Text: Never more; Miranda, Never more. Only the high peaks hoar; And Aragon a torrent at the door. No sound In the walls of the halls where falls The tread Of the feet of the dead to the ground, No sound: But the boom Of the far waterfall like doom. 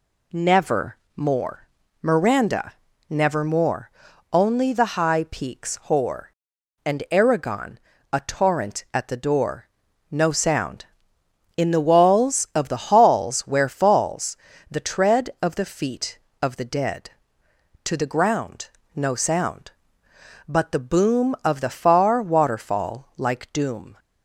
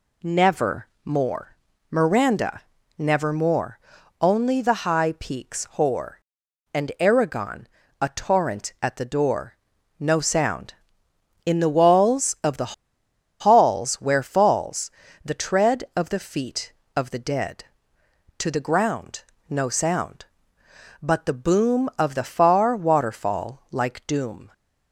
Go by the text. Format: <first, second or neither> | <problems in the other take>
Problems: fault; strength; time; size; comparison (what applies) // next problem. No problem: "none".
first | pauses between "Never" and "more"; slight; at 0.8 s; 0.16 s long; slight in the first // pauses between "Aragon" and "a"; slight; at 7.6 s; 0.32 s long; slight in the first // pauses between "the" and "halls"; noticeable; at 12.7 s; 0.68 s long // pauses between "falls" and "The"; slight; at 14.8 s; 0.36 s long; slight in the first